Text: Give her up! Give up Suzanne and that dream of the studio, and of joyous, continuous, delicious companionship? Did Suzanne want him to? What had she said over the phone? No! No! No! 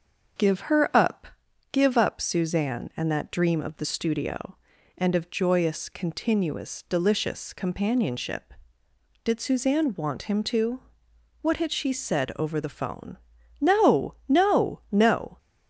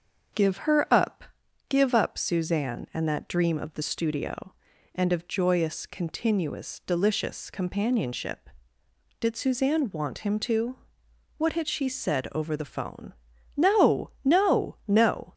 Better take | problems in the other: neither | starts louder than the rest; the same in both

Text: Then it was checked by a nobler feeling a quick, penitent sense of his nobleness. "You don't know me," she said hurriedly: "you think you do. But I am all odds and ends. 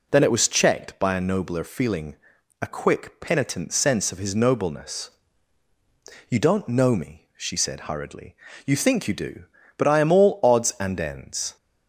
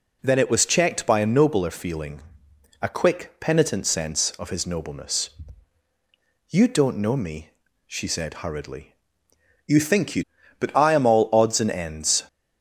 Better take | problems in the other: first | pauses between "feeling" and "a"; noticeable; at 2.2 s; 0.58 s long; also in the first // skips "do"; at 10.3 s

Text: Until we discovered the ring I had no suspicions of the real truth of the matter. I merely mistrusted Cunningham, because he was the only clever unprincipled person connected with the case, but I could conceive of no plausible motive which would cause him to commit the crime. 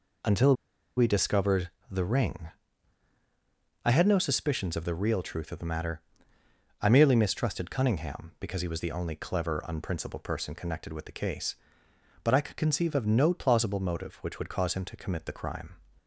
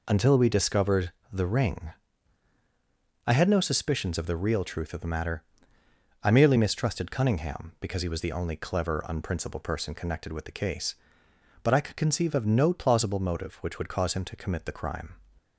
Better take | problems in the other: second | pauses between "Until" and "we"; at 0.5 s; 0.43 s long // pauses between "discovered" and "the"; slight; at 1.7 s; 0.20 s long; slight in the second // pauses between "ring" and "I"; strong; at 2.4 s; 1.3 s long; strong in the second

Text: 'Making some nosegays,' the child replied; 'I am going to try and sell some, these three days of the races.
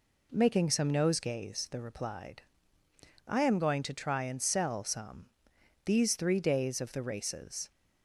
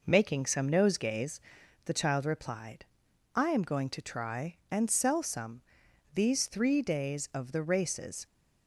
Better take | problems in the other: second | skips "child"; at 1.8 s

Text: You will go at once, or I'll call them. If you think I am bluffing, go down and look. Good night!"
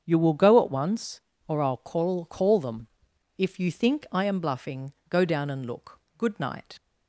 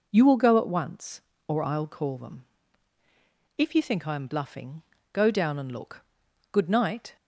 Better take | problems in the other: second | starts louder than the rest; strong; until 1.0 s; 7.5 dB // says "call" twice; at 2.2 s

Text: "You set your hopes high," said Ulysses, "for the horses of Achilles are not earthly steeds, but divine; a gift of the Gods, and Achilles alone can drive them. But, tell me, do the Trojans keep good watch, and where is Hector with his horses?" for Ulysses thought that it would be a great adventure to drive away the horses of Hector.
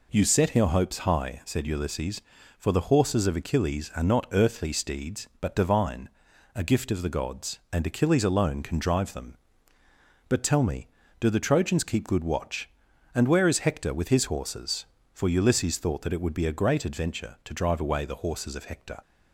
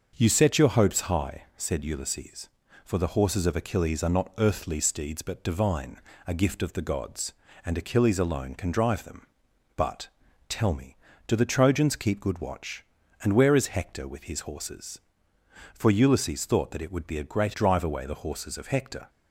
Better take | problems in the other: first | starts louder than the rest; until 1.1 s; 6.5 dB // skips "adventure to"; at 17.5 s

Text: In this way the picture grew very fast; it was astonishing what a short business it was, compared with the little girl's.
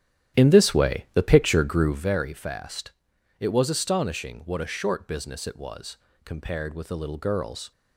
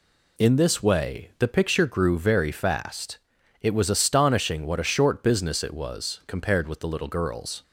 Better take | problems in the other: second | starts louder than the rest; strong; until 2.2 s; 11 dB

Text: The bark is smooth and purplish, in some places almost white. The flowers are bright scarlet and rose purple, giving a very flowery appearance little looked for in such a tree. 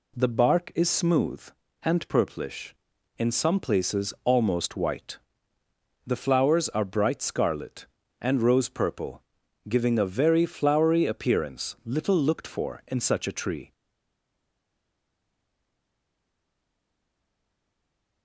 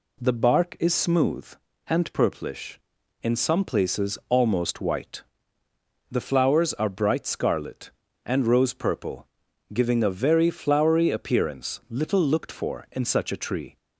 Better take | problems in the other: second | stays silent after the last word; strong; from 13.7 s on; 4.5 s long

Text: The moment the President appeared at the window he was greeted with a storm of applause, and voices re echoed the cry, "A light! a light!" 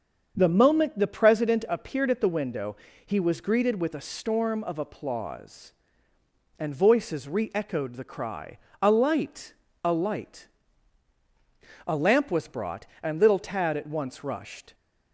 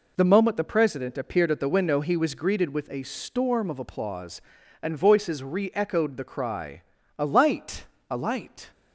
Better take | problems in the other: second | starts louder than the rest; until 1.3 s; 7 dB // pauses between "window" and "he"; slight; at 2.7 s; 0.28 s long // goes on to say "A lamp was brought and little Tad at once rushed"; strong; from 11.8 s on; 2.8 s long

